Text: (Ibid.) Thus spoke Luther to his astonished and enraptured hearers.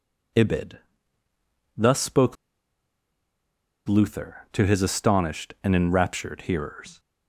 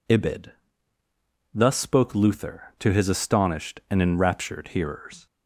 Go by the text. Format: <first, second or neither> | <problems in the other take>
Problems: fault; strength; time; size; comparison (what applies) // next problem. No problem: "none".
second | pauses between "spoke" and "Luther"; strong; at 2.3 s; 1.5 s long